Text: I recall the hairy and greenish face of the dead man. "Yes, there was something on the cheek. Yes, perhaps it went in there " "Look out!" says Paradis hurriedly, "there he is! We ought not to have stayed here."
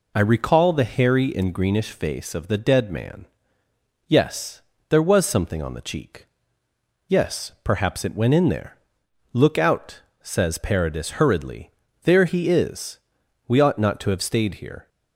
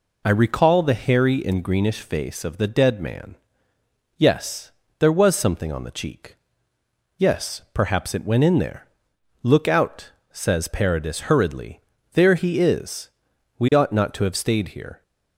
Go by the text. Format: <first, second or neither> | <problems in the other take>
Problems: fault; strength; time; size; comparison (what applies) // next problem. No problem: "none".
neither | none